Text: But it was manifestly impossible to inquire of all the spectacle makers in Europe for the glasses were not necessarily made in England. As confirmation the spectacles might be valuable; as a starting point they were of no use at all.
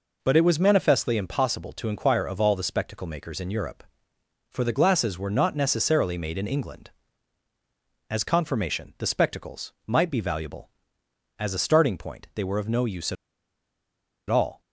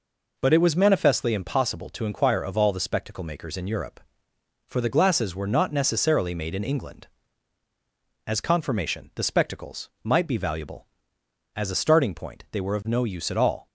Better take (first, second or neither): second